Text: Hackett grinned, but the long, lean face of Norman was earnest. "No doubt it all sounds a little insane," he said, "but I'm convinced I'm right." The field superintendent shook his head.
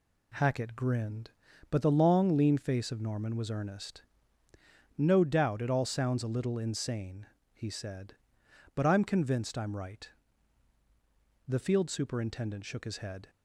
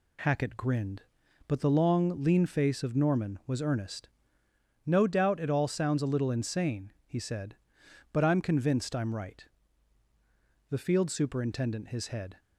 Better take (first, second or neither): first